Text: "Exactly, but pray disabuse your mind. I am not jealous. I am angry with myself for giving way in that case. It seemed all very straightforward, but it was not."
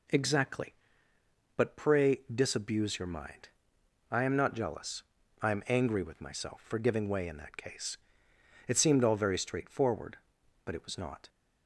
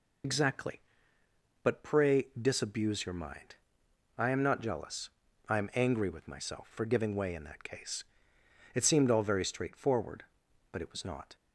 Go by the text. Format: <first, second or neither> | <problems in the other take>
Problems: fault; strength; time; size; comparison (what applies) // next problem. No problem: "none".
first | loses the start of "Exactly"; at 0.2 s; 85 ms